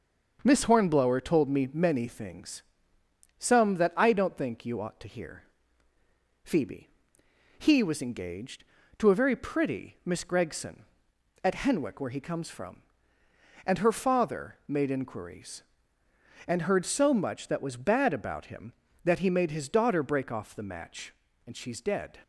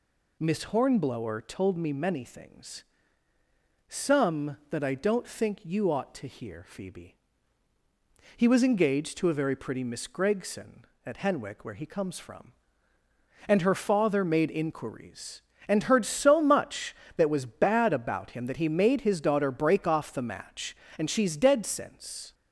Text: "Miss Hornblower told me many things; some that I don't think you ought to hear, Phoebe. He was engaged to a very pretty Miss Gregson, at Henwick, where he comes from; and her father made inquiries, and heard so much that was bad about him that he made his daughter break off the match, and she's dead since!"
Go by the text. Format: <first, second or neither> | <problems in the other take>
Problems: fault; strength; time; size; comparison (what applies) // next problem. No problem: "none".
second | starts louder than the rest; until 1.4 s; 6.5 dB // stops before "since"; at 22.2 s